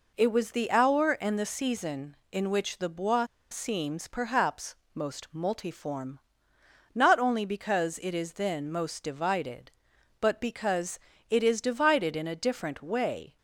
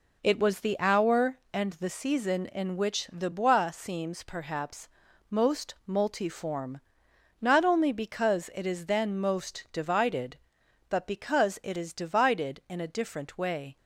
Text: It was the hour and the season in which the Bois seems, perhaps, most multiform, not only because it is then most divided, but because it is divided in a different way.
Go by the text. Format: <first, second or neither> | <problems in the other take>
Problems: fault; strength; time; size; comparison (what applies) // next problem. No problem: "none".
second | pauses between "Bois" and "seems"; slight; at 3.2 s; 0.26 s long // pauses between "because" and "it"; slight; at 10.9 s; 0.30 s long